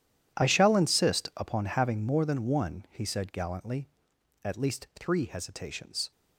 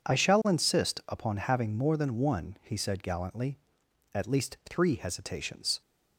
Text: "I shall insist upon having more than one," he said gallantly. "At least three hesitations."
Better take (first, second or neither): second